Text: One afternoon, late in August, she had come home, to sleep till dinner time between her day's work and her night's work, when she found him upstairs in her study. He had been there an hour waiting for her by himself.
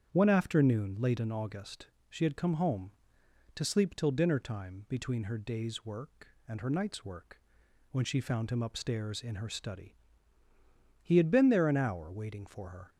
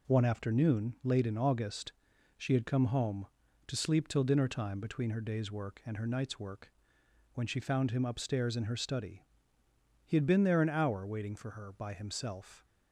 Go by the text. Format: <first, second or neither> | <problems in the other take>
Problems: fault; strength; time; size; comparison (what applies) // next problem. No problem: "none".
second | starts louder than the rest; strong; until 1.1 s; 8 dB // stops before "by himself"; at 12.8 s